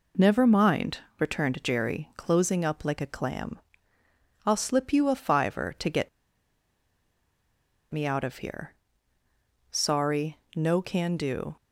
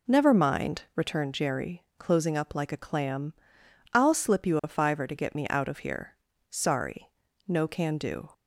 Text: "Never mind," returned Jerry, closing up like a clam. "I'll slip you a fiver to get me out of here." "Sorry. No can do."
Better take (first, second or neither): second